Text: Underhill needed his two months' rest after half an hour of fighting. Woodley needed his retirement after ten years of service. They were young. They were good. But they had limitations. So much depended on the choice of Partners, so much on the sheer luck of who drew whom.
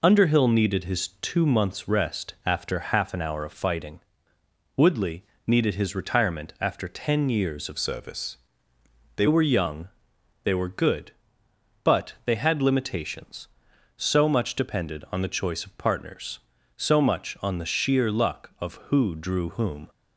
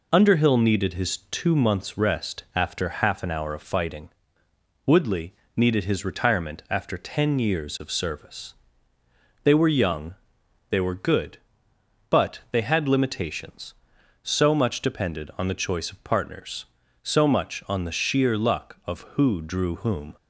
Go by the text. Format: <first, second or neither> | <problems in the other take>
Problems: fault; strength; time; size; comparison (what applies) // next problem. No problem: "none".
second | pauses between "Woodley" and "needed"; slight; at 5.2 s; 0.24 s long; slight in the second // changes voice from "service" to "They"; from 7.7 to 9.2 s; 1.5 s long